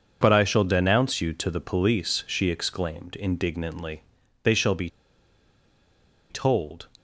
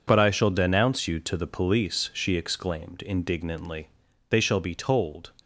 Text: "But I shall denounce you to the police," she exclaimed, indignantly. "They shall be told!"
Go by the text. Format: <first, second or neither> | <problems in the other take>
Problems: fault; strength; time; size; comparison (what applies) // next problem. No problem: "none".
second | pauses between "be" and "told"; strong; at 4.8 s; 1.4 s long